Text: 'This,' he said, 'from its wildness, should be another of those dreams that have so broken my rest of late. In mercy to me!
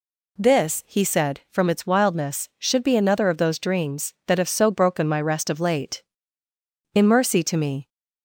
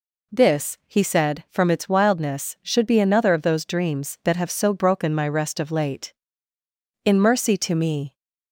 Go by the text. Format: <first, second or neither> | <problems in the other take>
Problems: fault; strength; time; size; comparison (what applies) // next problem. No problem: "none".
neither | none